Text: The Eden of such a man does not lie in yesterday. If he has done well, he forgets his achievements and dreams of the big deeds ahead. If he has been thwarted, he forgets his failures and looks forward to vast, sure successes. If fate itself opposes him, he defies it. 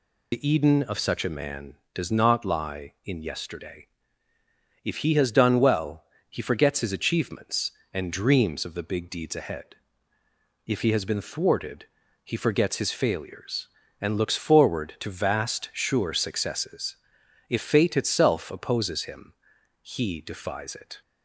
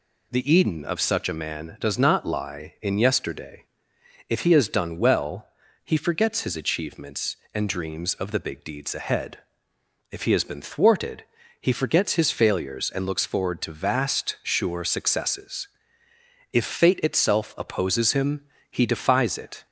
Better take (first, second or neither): second